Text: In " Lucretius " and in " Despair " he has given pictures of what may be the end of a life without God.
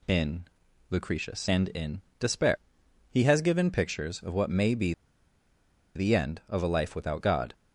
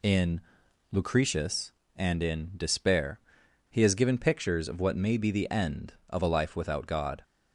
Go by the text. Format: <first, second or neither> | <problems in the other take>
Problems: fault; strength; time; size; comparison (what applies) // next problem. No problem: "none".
second | pauses between "be" and "the"; at 4.9 s; 1.0 s long